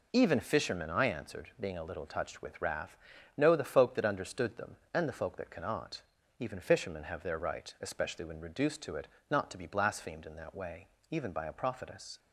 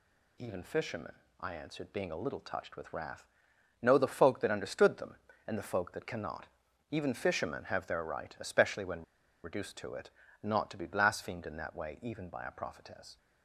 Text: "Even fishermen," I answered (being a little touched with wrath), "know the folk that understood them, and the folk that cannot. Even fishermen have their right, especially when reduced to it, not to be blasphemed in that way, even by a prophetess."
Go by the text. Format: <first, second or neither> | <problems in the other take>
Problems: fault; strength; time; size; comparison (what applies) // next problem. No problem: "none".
first | pauses between "when" and "reduced"; at 9.0 s; 0.42 s long